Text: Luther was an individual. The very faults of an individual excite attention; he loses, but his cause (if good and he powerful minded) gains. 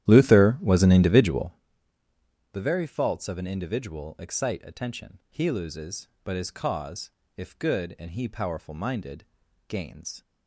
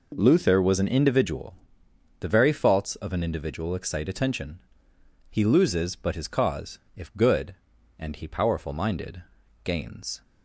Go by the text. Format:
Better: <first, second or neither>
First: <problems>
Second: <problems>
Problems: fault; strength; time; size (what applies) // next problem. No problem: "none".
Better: second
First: starts louder than the rest; strong; until 1.5 s; 12 dB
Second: none